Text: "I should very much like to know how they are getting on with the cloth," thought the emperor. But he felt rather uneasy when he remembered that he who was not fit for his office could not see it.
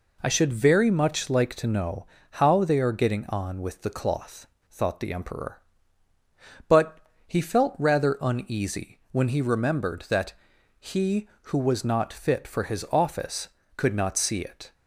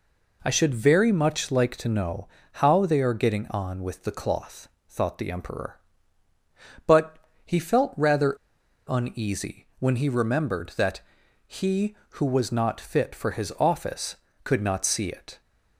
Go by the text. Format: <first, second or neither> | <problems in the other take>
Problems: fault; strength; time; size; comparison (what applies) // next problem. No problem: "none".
first | pauses between "know" and "how"; slight; at 2.2 s; 0.26 s long; slight in the first // pauses between "But" and "he"; slight; at 7.1 s; 0.26 s long; slight in the first // pauses between "rather" and "uneasy"; noticeable; at 8.3 s; 0.51 s long // pauses between "that" and "he"; noticeable; at 11.0 s; 0.46 s long; noticeable in the first